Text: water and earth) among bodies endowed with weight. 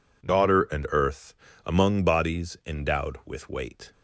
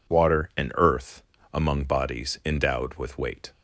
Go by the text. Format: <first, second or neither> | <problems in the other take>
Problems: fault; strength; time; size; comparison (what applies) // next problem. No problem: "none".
second | says "daughter" for "water"; at 0.2 s